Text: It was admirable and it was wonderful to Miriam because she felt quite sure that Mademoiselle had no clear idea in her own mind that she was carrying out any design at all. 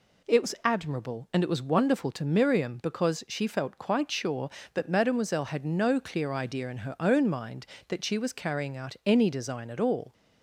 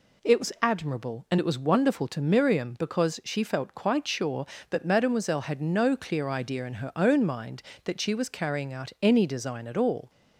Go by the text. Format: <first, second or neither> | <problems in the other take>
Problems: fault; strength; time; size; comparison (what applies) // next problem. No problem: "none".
neither | none